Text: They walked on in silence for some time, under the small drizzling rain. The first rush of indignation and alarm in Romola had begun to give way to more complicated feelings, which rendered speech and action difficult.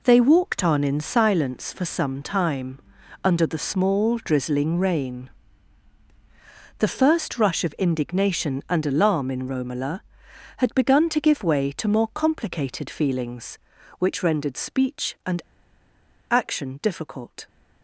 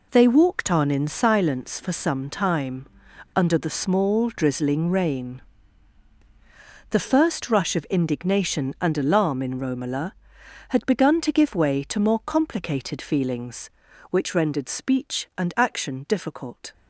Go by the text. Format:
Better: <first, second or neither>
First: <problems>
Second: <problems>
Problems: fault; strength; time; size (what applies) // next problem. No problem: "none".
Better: second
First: pauses between "and" and "action"; noticeable; at 15.3 s; 0.91 s long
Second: none